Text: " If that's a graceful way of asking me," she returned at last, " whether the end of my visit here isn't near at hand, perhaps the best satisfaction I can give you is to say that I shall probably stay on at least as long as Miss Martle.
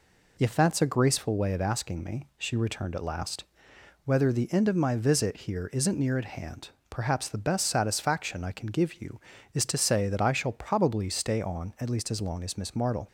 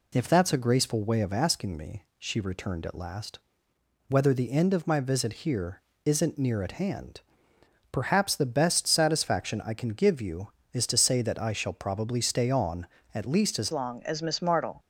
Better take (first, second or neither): first